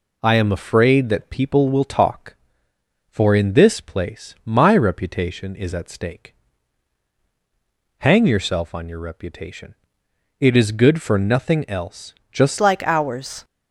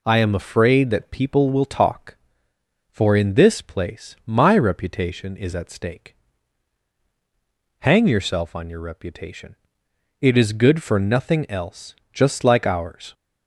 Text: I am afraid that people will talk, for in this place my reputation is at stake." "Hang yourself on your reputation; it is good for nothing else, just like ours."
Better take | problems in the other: second | changes voice at "like"; from 12.5 s on; 0.9 s long

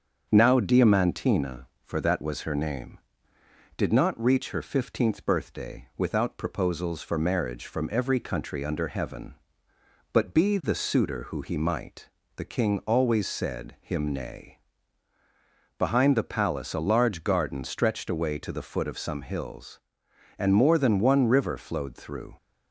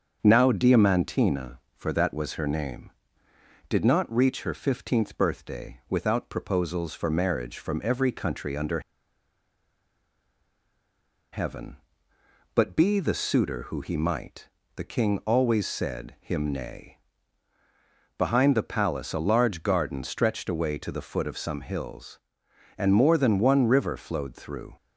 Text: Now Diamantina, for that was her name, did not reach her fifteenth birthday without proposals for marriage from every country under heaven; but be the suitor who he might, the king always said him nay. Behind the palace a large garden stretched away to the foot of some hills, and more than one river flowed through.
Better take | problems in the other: first | starts louder than the rest; until 1.2 s; 7 dB; also in the first // pauses between "under" and "heaven"; strong; at 8.7 s; 2.5 s long

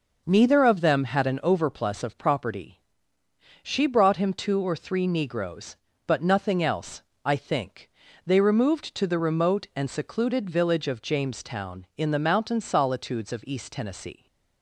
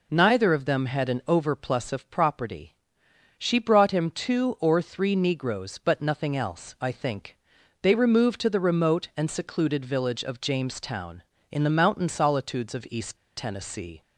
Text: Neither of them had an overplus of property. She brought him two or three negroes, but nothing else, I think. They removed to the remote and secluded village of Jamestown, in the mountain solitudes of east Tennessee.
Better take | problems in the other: first | pauses between "east" and "Tennessee"; slight; at 13.1 s; 0.19 s long

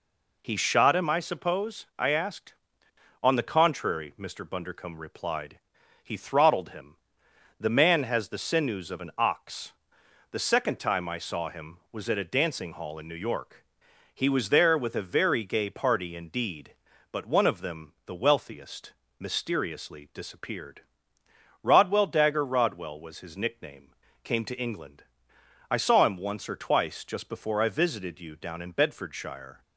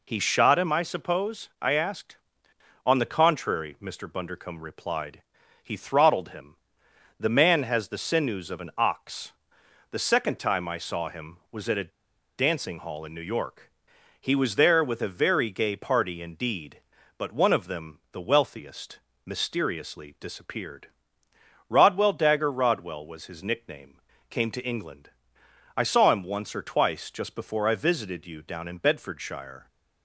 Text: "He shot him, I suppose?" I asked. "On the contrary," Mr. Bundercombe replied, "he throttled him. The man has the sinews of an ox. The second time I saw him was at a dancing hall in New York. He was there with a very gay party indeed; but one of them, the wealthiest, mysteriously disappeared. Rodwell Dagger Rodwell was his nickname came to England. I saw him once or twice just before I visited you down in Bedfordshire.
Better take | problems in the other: first | pauses between "a" and "dancing"; noticeable; at 11.9 s; 0.46 s long // pauses between "nickname" and "came"; slight; at 24.0 s; 0.30 s long; slight in the first

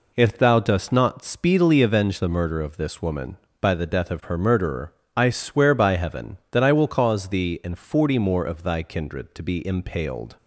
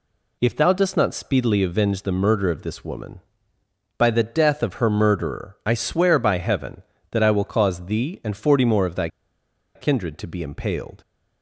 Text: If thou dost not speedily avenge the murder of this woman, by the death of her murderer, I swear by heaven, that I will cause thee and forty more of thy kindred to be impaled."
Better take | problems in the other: first | pauses between "thy" and "kindred"; noticeable; at 9.0 s; 0.67 s long

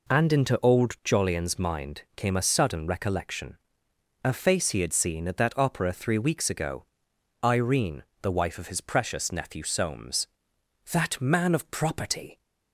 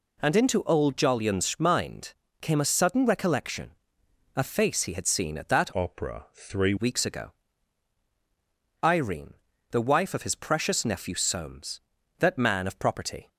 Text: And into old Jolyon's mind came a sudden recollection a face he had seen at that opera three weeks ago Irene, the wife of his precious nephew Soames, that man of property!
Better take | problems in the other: first | pauses between "mind" and "came"; slight; at 2.1 s; 0.28 s long // pauses between "recollection" and "a"; noticeable; at 3.7 s; 0.64 s long; noticeable in the first // changes voice from "opera" to "three"; from 5.7 to 6.7 s; 1.0 s long // pauses between "ago" and "Irene"; strong; at 7.3 s; 1.5 s long; noticeable in the first

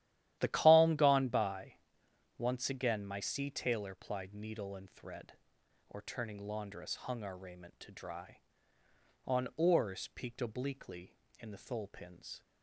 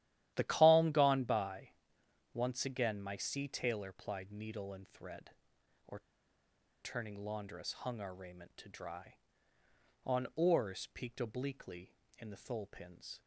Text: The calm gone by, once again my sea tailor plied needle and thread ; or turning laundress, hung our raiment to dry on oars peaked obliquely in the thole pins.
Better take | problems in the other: first | starts louder than the rest; strong; until 1.3 s; 12.5 dB; strong in the first // pauses between "or" and "turning"; noticeable; at 5.9 s; 0.82 s long

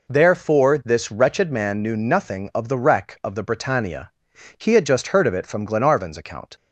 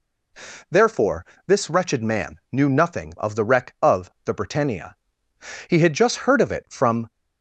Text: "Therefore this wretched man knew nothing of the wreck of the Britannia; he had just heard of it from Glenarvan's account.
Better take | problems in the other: first | pauses between "Therefore" and "this"; slight; at 1.2 s; 0.20 s long // stops before "Glenarvan's account"; at 7.0 s

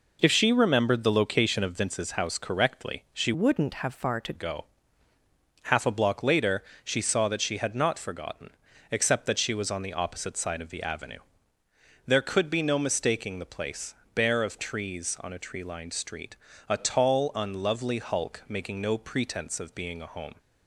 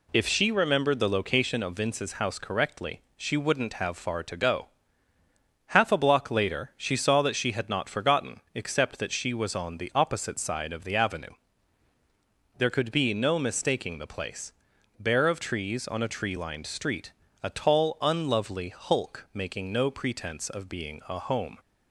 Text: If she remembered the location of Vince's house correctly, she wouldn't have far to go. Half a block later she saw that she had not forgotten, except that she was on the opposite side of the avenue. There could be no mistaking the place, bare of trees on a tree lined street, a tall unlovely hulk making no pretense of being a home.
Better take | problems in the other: second | changes voice from "wouldn't" to "to"; from 3.3 to 4.3 s; 1.0 s long // pauses between "later" and "she"; slight; at 6.6 s; 0.22 s long

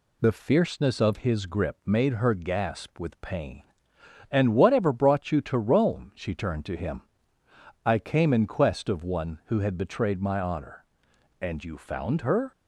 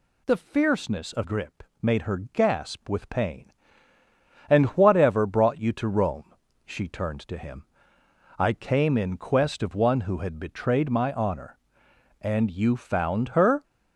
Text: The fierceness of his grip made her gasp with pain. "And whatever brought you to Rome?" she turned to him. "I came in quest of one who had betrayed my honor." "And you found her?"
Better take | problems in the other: first | skips "his"; at 1.2 s // pauses between "grip" and "made"; slight; at 1.6 s; 0.18 s long

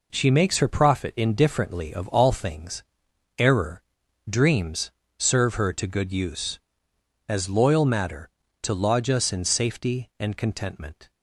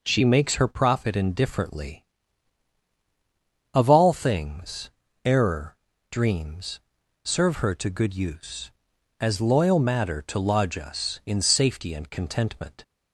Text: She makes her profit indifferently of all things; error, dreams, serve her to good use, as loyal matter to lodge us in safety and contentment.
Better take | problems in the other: neither | none

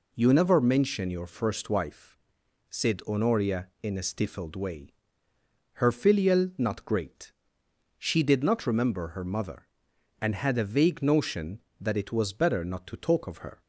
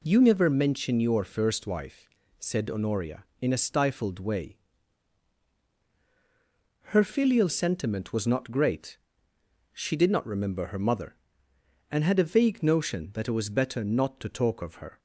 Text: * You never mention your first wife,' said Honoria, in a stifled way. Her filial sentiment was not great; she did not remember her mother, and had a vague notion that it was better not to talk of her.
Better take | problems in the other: second | skips "sentiment was"; at 6.5 s

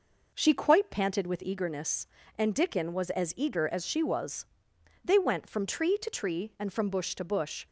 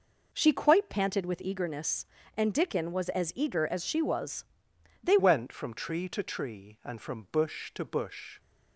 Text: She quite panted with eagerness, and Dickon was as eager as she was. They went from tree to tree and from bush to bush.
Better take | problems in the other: first | changes voice at "went"; from 5.1 s on; 3.2 s long

